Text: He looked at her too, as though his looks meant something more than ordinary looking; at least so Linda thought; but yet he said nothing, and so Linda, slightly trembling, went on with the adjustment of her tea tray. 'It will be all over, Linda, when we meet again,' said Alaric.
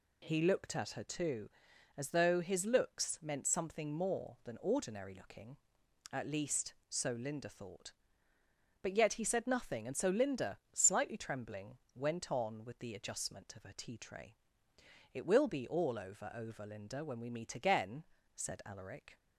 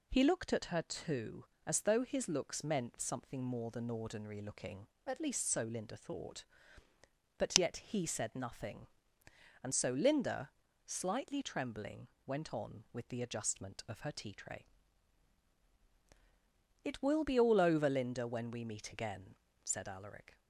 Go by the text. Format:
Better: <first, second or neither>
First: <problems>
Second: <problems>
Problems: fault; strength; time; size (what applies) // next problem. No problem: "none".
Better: second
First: says "over" twice; at 16.3 s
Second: none